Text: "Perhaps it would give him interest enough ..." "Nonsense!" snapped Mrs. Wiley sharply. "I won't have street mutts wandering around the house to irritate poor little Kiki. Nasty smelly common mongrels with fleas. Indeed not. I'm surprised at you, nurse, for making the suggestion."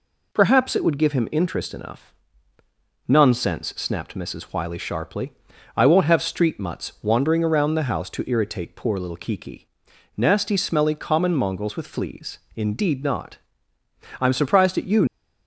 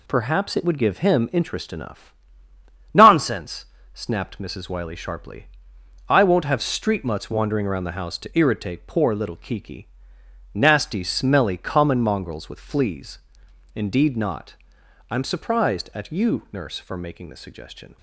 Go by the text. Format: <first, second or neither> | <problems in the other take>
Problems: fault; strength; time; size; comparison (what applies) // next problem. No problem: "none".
second | stops before "nurse for making the suggestion"; at 15.0 s